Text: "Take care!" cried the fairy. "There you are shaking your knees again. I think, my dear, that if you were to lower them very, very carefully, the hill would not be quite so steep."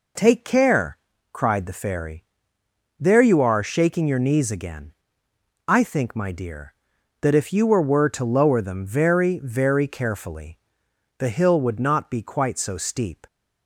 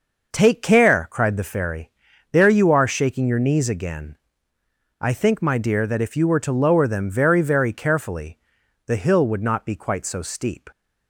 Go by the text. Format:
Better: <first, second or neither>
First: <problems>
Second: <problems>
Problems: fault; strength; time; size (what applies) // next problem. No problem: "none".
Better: second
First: says "were" twice; at 7.8 s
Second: none